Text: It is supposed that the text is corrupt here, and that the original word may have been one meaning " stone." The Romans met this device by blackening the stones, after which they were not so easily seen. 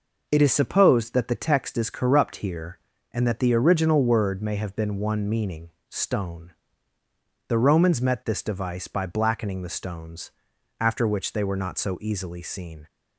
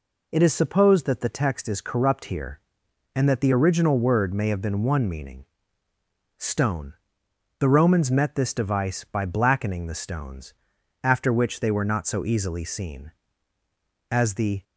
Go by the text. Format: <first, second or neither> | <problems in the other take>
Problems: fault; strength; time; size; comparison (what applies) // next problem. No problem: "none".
first | goes on to say "As the"; from 14.0 s on; 0.54 s long